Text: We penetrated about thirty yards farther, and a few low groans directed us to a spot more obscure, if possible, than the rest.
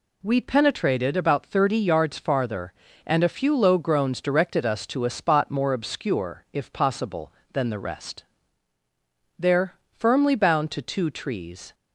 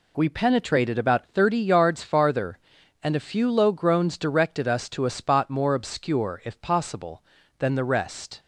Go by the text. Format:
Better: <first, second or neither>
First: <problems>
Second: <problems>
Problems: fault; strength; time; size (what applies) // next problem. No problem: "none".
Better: second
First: goes on to say "There firmly bound to two trees"; strong; from 9.3 s on; 2.3 s long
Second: none